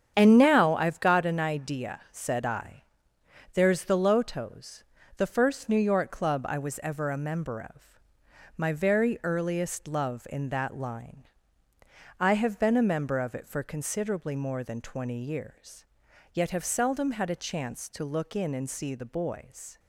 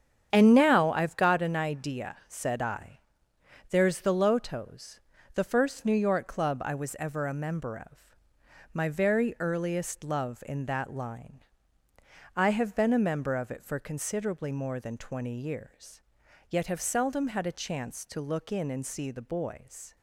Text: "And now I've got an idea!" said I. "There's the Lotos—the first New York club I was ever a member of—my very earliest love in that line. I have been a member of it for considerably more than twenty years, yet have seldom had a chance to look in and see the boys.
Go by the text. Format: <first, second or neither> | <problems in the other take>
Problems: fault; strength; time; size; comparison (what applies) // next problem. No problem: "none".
neither | starts louder than the rest; strong; the same in both